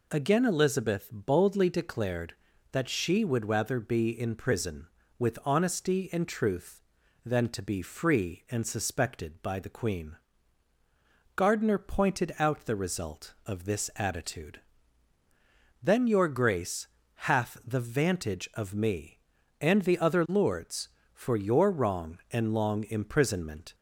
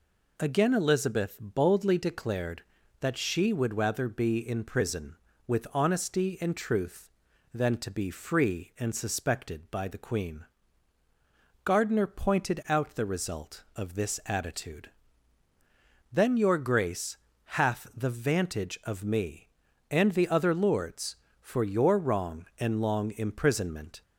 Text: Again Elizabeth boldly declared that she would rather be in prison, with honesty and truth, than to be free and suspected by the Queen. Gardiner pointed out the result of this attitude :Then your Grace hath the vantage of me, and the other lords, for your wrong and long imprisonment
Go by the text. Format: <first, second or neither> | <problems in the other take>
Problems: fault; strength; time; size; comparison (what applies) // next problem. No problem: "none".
neither | pauses between "Grace" and "hath"; the same in both